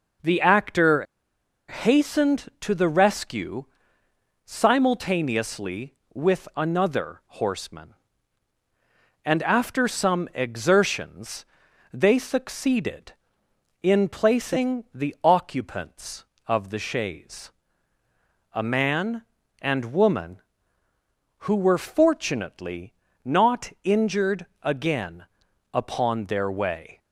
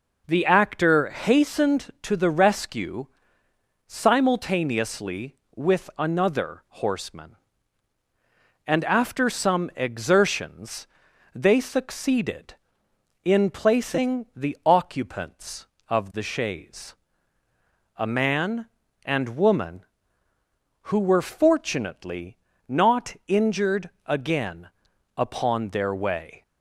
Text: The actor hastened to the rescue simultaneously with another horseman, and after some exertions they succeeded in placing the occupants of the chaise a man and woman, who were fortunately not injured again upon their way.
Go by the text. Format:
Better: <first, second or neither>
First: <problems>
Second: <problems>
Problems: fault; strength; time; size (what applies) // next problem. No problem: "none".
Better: second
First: pauses between "actor" and "hastened"; noticeable; at 1.0 s; 0.64 s long // pauses between "rescue" and "simultaneously"; noticeable; at 3.6 s; 0.80 s long // pauses between "exertions" and "they"; noticeable; at 11.4 s; 0.48 s long // pauses between "chaise" and "a"; at 17.5 s; 1.0 s long // pauses between "fortunately" and "not"; slight; at 22.9 s; 0.32 s long // pauses between "injured" and "again"; slight; at 24.4 s; 0.18 s long // pauses between "again" and "upon"; noticeable; at 25.2 s; 0.48 s long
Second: pauses between "rescue" and "simultaneously"; noticeable; at 3.0 s; 0.80 s long // pauses between "exertions" and "they"; noticeable; at 10.8 s; 0.48 s long // pauses between "chaise" and "a"; at 16.9 s; 1.0 s long // pauses between "fortunately" and "not"; slight; at 22.3 s; 0.32 s long // pauses between "injured" and "again"; slight; at 23.8 s; 0.18 s long // pauses between "again" and "upon"; noticeable; at 24.6 s; 0.48 s long